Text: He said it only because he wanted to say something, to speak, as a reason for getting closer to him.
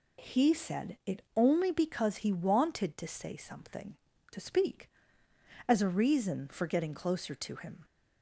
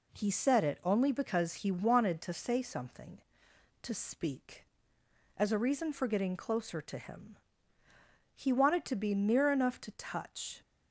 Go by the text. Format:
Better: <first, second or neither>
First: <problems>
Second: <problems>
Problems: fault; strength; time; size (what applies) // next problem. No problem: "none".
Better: first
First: none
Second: goes on to say "He wanted to be near enough to touch"; strong; from 8.3 s on; 2.2 s long